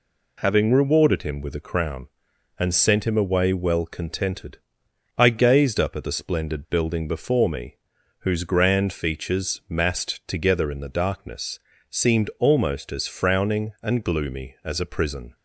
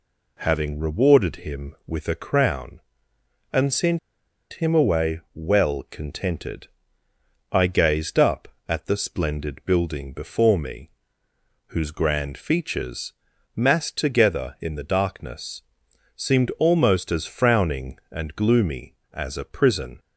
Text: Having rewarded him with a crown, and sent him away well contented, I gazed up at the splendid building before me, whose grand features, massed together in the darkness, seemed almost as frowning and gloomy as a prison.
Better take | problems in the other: first | pauses between "sent" and "him"; noticeable; at 3.9 s; 0.54 s long // pauses between "away" and "well"; slight; at 5.1 s; 0.16 s long

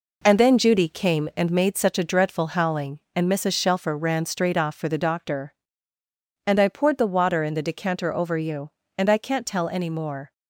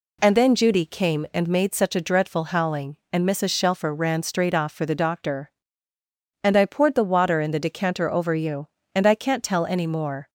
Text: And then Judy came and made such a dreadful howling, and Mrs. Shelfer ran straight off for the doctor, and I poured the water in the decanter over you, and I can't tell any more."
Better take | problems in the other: second | gets quieter; throughout; 6.5 dB

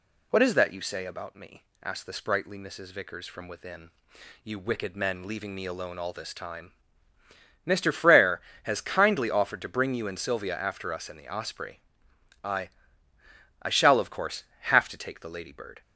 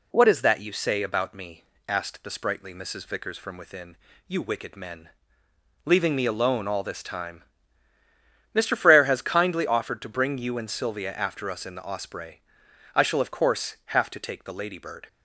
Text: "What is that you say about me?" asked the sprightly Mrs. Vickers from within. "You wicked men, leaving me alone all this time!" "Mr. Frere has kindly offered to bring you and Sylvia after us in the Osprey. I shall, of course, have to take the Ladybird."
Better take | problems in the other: second | says "I" twice; at 13.6 s

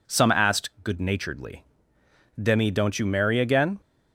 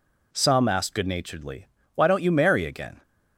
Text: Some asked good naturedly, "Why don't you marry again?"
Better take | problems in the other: second | says "Demi" for "Why"; at 2.4 s

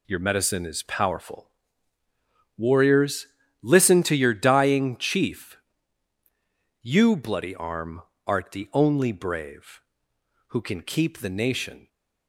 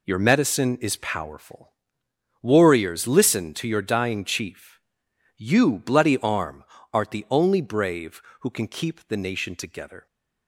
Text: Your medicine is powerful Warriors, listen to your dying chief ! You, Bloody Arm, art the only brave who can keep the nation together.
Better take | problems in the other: second | pauses between "powerful" and "Warriors"; at 1.4 s; 1.0 s long; noticeable in the second // stops before "together"; at 11.8 s

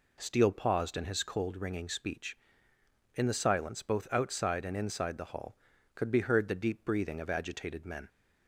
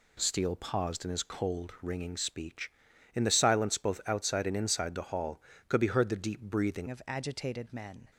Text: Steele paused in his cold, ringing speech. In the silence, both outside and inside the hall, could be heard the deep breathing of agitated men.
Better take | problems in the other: first | changes voice at "of"; from 6.8 s on; 1.2 s long

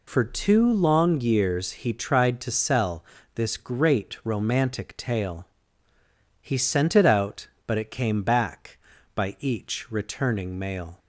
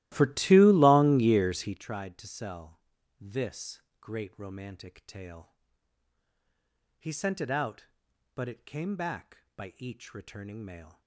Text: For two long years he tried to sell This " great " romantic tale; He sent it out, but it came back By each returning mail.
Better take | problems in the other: first | starts louder than the rest; strong; until 1.8 s; 16 dB // pauses between "sell" and "This"; at 2.8 s; 0.38 s long; slight in the first

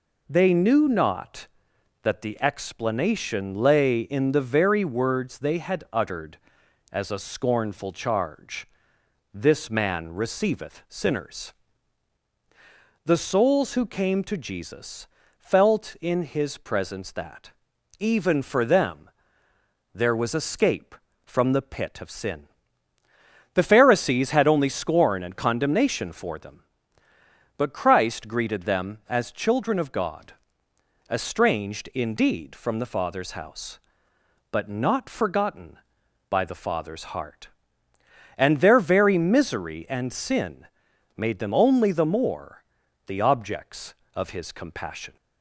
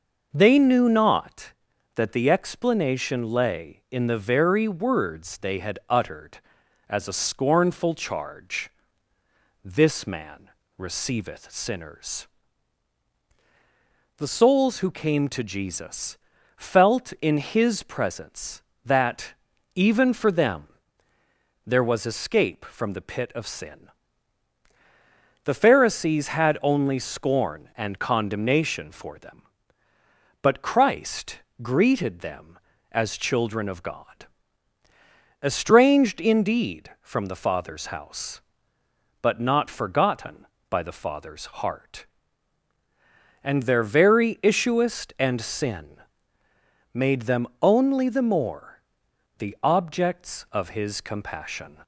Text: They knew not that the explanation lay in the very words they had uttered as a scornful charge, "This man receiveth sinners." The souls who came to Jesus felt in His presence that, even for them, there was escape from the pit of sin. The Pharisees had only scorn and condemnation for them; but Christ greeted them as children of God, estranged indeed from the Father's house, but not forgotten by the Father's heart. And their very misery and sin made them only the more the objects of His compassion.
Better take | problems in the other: first | pauses between "man" and "receiveth"; slight; at 10.5 s; 0.26 s long // pauses between "Jesus" and "felt"; at 16.1 s; 0.40 s long; slight in the first // pauses between "Christ" and "greeted"; slight; at 31.4 s; 0.20 s long // says "issuest" for "misery"; at 44.4 s // pauses between "sin" and "made"; noticeable; at 46.0 s; 0.92 s long; noticeable in the first // pauses between "more" and "the"; noticeable; at 48.8 s; 0.58 s long; also in the first

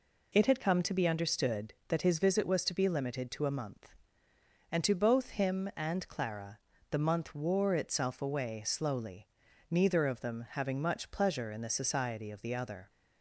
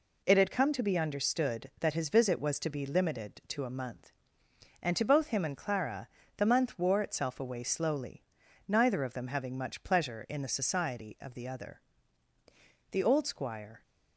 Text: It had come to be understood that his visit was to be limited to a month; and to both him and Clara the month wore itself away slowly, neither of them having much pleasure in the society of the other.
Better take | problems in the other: first | pauses between "Clara" and "the"; slight; at 6.0 s; 0.30 s long; slight in the first // goes on to say "The old squire"; noticeable; from 12.9 s on; 0.90 s long

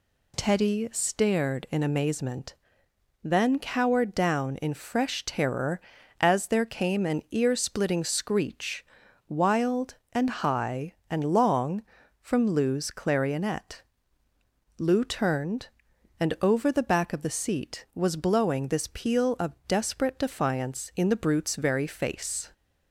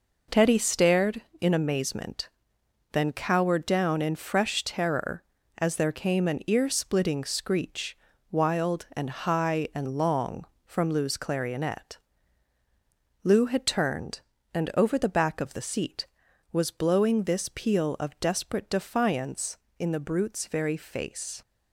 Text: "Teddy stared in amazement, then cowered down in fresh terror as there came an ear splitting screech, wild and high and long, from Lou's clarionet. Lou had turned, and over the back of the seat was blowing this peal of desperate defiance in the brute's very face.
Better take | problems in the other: second | skips "had"; at 15.0 s

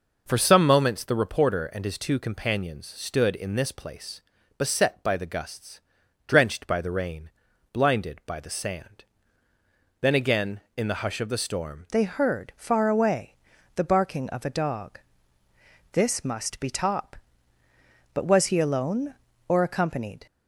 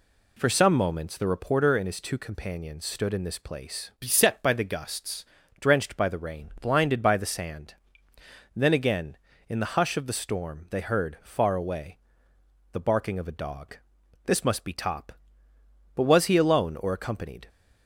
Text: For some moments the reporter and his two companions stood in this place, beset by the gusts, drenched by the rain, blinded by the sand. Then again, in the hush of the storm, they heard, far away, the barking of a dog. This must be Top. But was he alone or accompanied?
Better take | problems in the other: second | changes voice at "they"; from 11.9 s on; 8.3 s long

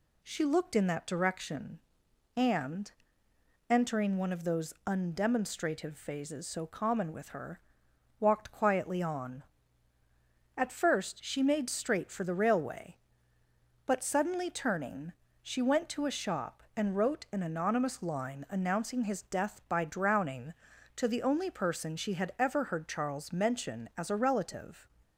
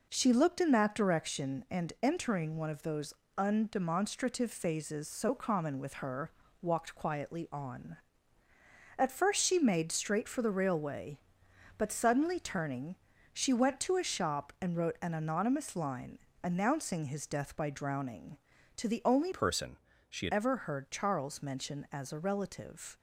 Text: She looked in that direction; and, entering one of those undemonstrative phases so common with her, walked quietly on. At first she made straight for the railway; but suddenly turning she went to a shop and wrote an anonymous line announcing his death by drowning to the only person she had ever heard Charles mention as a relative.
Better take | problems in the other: first | pauses between "those" and "undemonstrative"; slight; at 3.1 s; 0.24 s long // pauses between "turning" and "she"; at 12.9 s; 0.38 s long; slight in the first // pauses between "line" and "announcing"; slight; at 16.1 s; 0.24 s long // changes voice from "person" to "had"; from 19.3 to 20.3 s; 1.0 s long // pauses between "person" and "she"; slight; at 19.7 s; 0.32 s long

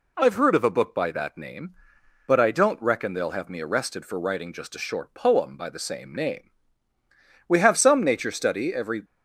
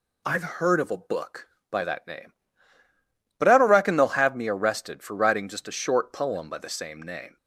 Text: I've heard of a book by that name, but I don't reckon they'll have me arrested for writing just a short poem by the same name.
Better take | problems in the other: second | goes on to say "We have some nature study every"; from 7.4 s on; 1.5 s long

